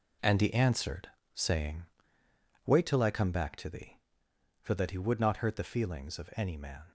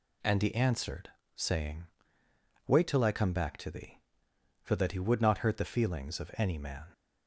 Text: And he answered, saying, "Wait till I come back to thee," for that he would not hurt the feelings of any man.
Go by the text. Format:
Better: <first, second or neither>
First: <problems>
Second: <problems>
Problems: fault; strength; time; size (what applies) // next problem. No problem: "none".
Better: second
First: gets quieter; strong; throughout; 9 dB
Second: none